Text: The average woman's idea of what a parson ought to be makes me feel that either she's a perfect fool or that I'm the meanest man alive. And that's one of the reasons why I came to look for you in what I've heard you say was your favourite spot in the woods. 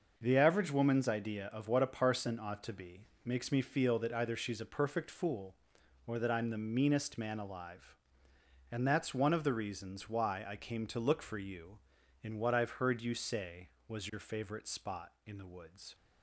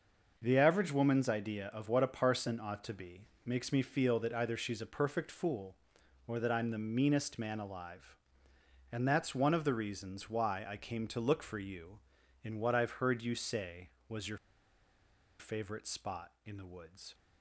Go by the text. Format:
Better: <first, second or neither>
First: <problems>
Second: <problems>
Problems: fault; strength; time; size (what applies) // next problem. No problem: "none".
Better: first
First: pauses between "be" and "makes"; slight; at 3.0 s; 0.18 s long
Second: pauses between "be" and "makes"; slight; at 3.2 s; 0.18 s long // pauses between "your" and "favourite"; at 14.3 s; 1.0 s long